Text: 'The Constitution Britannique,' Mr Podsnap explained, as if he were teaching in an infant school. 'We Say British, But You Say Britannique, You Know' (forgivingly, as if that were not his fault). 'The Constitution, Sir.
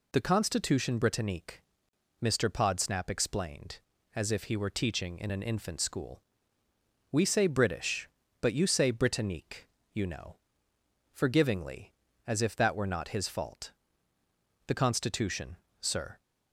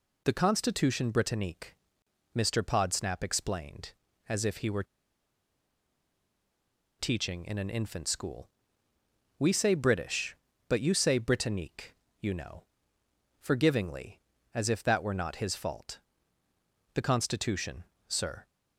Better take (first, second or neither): first